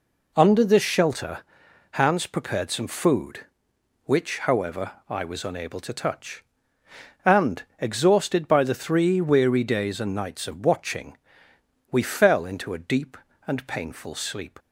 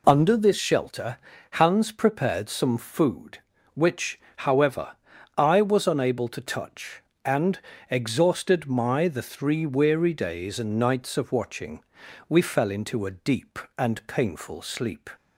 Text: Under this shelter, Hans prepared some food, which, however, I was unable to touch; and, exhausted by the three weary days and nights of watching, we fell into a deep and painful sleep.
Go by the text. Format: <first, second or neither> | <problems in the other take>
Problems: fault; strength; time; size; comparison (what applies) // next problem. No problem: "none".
first | says "my" for "by"; at 8.6 s